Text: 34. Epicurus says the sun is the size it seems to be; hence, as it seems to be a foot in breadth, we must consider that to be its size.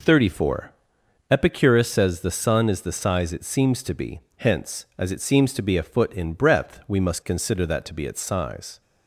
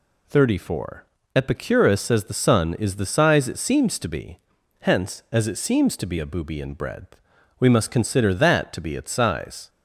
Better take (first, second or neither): first